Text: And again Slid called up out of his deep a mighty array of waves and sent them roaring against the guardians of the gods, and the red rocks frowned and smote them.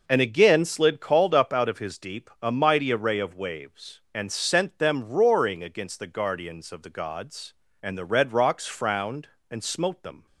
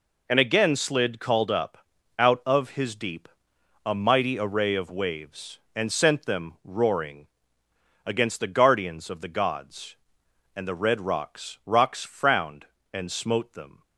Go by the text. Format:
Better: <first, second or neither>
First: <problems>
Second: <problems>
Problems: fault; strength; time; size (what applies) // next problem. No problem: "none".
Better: first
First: none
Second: pauses between "up" and "out"; at 1.7 s; 0.42 s long // pauses between "deep" and "a"; noticeable; at 3.2 s; 0.56 s long // pauses between "roaring" and "against"; noticeable; at 7.2 s; 0.78 s long // says "rocks" twice; at 11.6 s